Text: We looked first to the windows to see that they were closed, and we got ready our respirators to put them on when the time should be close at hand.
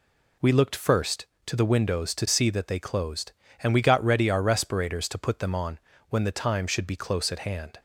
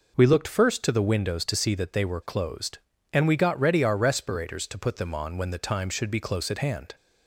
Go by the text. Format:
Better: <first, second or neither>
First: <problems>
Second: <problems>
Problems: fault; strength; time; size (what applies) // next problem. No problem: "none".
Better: second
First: skips "were"; at 2.7 s // pauses between "on" and "when"; slight; at 5.7 s; 0.32 s long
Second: none